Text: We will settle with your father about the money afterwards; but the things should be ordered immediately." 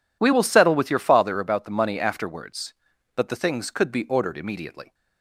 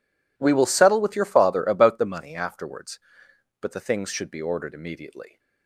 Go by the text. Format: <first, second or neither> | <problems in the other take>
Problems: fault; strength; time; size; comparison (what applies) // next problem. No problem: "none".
second | says "could" for "should"; at 3.6 s